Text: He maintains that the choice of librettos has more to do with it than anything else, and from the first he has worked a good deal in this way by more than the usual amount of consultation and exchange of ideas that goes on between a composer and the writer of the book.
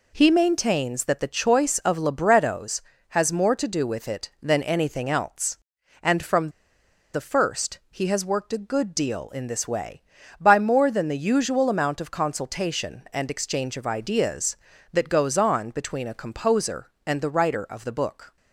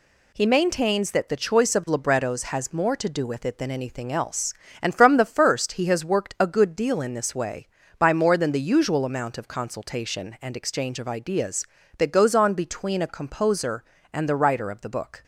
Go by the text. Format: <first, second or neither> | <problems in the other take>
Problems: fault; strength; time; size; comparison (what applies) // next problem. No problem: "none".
second | pauses between "from" and "the"; noticeable; at 6.5 s; 0.63 s long